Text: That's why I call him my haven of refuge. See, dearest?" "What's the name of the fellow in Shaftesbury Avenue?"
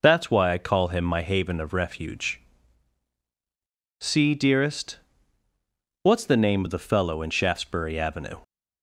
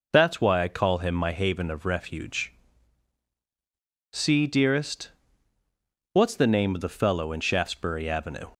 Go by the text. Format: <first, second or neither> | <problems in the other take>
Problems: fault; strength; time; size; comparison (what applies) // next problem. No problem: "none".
neither | none